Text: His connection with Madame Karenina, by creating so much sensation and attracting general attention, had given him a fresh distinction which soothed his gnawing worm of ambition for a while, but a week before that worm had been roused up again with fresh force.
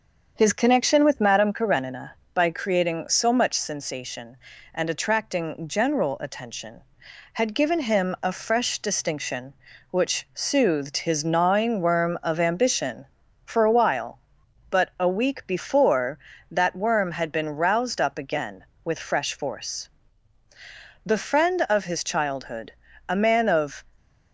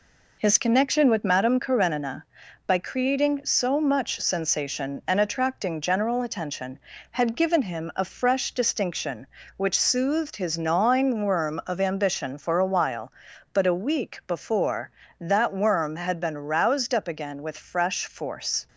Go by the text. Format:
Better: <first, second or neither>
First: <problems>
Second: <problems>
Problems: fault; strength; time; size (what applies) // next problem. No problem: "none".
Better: second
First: starts louder than the rest; until 1.3 s; 7 dB // goes on to say "The friend of his childhood a man of"; strong; from 21.0 s on; 2.8 s long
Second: none